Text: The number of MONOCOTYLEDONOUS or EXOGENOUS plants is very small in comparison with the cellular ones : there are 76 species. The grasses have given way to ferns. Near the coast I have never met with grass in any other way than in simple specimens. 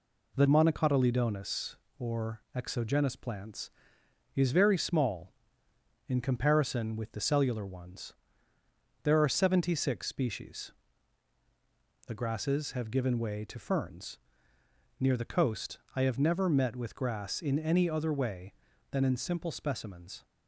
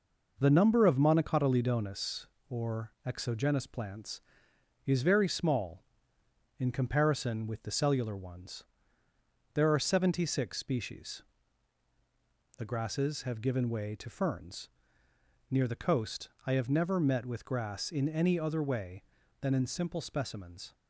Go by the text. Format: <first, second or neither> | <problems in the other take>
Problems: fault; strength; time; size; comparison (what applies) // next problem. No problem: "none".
second | skips "number of"; at 0.4 s // pauses between "coast" and "I"; slight; at 15.7 s; 0.16 s long; slight in the second